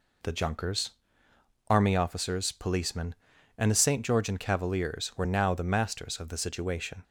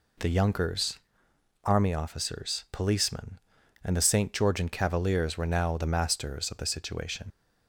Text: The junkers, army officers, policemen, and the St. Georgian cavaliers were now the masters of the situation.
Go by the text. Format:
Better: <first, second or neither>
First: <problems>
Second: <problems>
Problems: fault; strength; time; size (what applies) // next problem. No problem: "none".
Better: first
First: none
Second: leaves "situation" unfinished; at 7.3 s; 85 ms